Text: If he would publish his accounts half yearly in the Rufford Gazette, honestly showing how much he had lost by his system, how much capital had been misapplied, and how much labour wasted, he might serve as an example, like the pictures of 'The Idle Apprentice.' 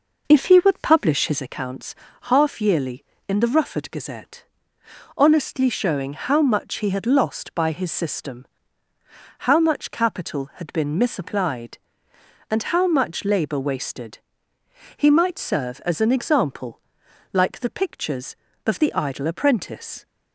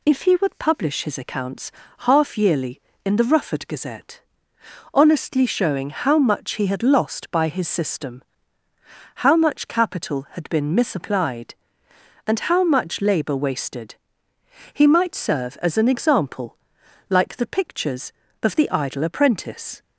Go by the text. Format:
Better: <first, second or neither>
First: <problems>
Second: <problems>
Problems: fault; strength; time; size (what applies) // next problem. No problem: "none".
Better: second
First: starts louder than the rest; noticeable; until 1.5 s; 5 dB // pauses between "accounts" and "half"; slight; at 1.9 s; 0.30 s long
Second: pauses between "accounts" and "half"; slight; at 1.6 s; 0.30 s long